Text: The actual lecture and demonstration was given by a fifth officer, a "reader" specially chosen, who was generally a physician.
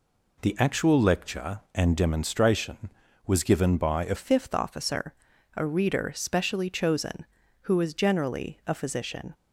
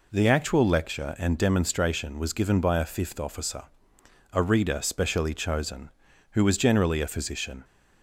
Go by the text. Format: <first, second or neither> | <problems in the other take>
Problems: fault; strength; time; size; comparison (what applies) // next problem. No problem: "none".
second | changes voice at "fifth"; from 4.1 s on; 5.2 s long